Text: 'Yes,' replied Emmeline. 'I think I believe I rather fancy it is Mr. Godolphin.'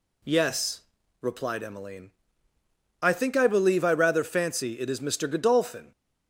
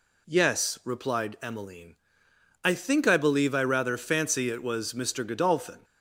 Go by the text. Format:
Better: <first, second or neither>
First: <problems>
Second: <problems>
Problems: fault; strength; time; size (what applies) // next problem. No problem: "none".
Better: first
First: none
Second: says "was" for "is"; at 4.6 s